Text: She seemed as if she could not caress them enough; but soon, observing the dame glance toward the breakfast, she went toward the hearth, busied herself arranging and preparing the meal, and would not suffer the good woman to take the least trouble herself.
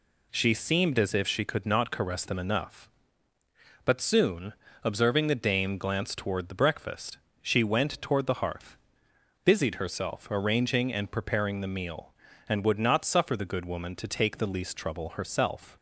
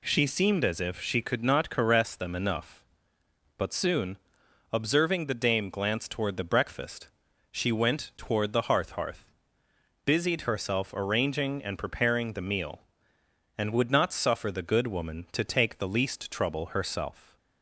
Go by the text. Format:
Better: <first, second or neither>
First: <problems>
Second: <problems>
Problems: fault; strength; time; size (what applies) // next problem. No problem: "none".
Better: first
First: none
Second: says "hearth" twice; at 8.9 s